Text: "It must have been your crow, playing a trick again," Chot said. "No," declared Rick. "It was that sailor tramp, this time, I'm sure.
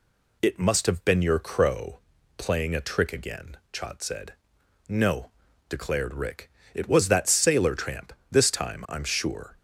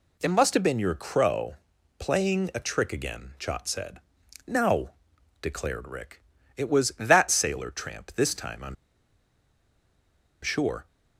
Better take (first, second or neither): first